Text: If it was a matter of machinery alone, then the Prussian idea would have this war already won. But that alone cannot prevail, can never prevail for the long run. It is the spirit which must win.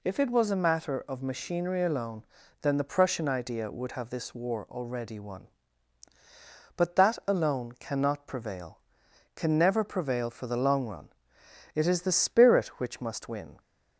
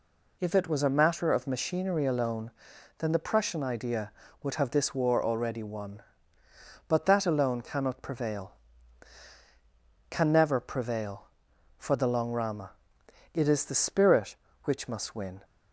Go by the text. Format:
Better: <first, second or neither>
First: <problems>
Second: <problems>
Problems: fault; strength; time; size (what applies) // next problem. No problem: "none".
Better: first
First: none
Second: says "rama" for "run"; at 12.3 s